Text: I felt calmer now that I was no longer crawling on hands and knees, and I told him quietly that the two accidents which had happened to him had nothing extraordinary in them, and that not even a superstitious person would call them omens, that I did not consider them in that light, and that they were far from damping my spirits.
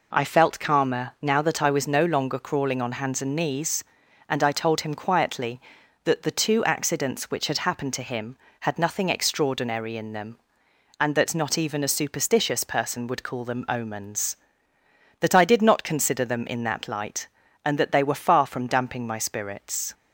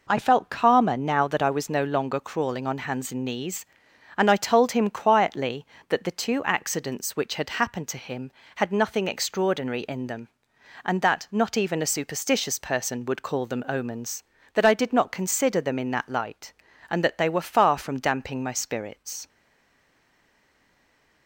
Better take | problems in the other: first | stays silent after the last word; noticeable; from 19.2 s on; 2.0 s long

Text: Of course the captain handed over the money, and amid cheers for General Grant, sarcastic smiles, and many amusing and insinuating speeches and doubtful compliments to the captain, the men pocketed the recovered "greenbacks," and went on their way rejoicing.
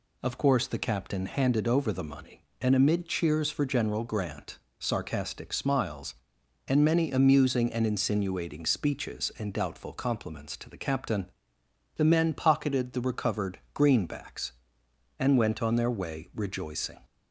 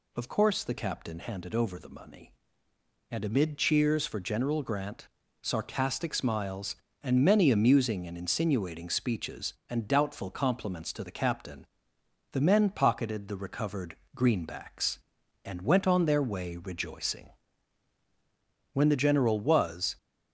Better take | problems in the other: first | pauses between "recovered" and "greenbacks"; slight; at 13.9 s; 0.18 s long // goes on to say "When the General was"; noticeable; from 18.6 s on; 1.2 s long

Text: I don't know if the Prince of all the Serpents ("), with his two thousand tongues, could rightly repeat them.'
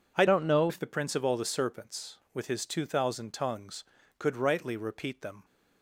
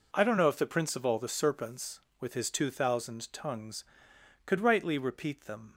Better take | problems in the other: second | changes voice from "don't" to "know"; from 0.2 to 0.7 s; 0.5 s long

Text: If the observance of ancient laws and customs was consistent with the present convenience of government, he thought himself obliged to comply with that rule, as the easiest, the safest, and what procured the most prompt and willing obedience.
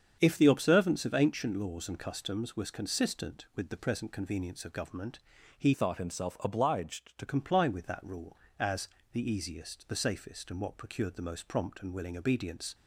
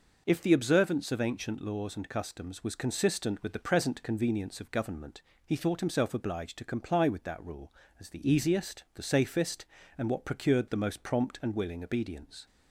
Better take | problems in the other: second | starts louder than the rest; strong; until 1.2 s; 7.5 dB // changes voice from "thought" to "to"; from 5.7 to 7.2 s; 1.5 s long // pauses between "as" and "the"; slight; at 8.8 s; 0.24 s long

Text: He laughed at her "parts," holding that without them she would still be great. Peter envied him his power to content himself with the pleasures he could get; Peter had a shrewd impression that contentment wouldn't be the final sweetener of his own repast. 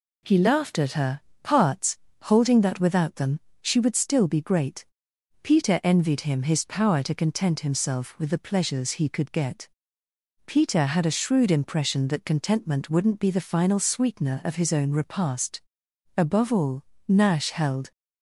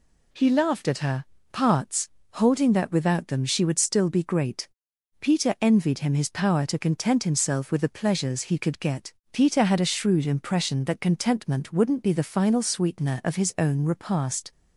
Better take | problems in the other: second | pauses between "her" and "parts"; slight; at 1.1 s; 0.24 s long; slight in the second // pauses between "them" and "she"; slight; at 3.4 s; 0.20 s long // goes on to say "Above all Nash held"; strong; from 16.1 s on; 1.7 s long

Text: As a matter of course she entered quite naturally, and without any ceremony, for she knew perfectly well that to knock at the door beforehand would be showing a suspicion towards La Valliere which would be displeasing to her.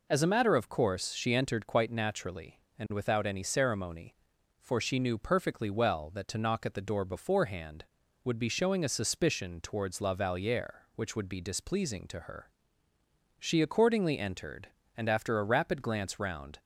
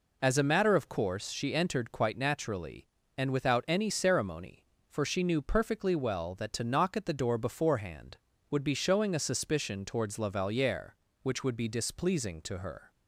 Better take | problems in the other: second | goes on to say "She accordingly entered and after a rapid glance round"; strong; from 13.3 s on; 3.2 s long

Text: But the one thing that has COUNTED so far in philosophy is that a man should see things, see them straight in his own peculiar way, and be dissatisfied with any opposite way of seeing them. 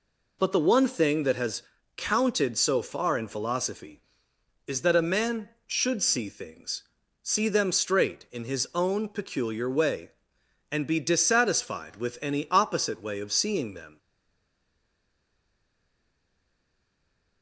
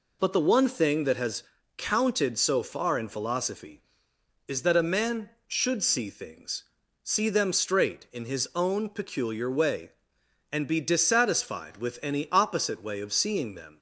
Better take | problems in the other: second | pauses between "has" and "COUNTED"; slight; at 1.6 s; 0.36 s long; slight in the second // stays silent after the last word; strong; from 13.9 s on; 3.5 s long

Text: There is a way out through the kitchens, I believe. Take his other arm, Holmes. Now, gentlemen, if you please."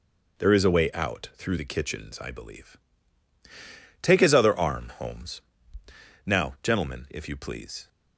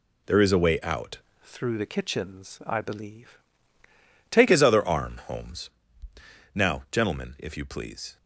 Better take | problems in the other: first | changes voice from "through" to "Take"; from 1.4 to 4.4 s; 3.0 s long

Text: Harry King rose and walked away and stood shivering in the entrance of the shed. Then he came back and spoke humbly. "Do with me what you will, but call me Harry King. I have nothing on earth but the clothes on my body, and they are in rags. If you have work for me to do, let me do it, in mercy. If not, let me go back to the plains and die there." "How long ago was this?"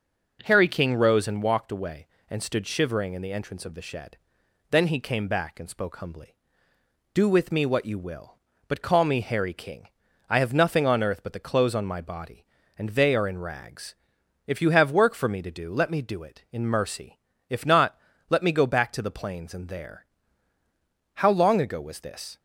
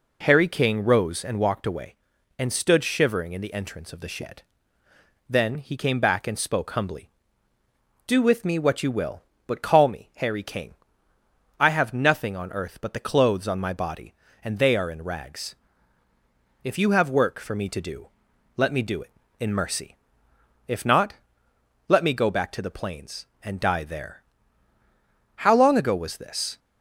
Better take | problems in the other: second | skips "die"; at 19.6 s

